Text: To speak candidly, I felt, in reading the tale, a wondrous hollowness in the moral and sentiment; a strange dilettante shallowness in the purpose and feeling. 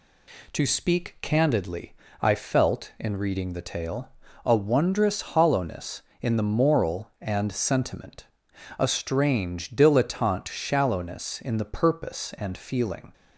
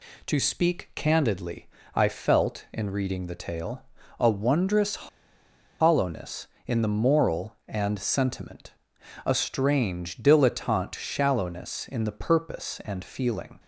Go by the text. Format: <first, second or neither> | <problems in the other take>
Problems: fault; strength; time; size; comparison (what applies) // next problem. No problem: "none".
first | pauses between "wondrous" and "hollowness"; noticeable; at 4.9 s; 0.83 s long